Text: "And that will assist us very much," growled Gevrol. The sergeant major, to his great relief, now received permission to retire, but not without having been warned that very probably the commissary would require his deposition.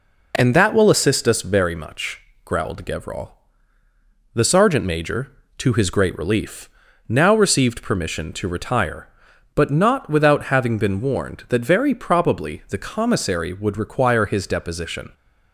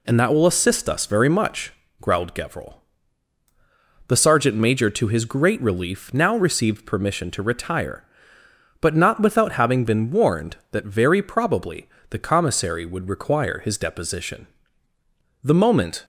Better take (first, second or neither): first